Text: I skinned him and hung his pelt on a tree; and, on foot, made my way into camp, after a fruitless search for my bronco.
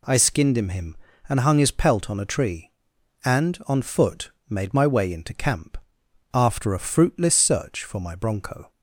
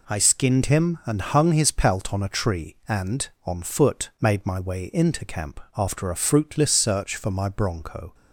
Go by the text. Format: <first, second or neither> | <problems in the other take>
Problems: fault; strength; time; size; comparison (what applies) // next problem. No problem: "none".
second | says "him" twice; at 0.6 s